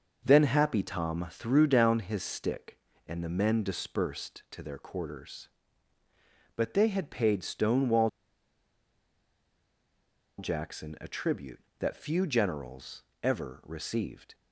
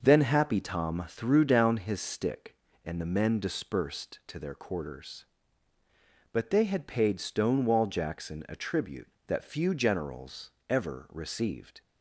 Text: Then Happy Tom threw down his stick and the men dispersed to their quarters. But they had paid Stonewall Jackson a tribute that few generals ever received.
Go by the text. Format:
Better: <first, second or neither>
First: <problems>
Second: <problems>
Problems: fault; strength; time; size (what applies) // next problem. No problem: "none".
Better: second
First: pauses between "Stonewall" and "Jackson"; strong; at 8.0 s; 2.3 s long // pauses between "generals" and "ever"; slight; at 13.0 s; 0.18 s long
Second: pauses between "generals" and "ever"; slight; at 10.5 s; 0.16 s long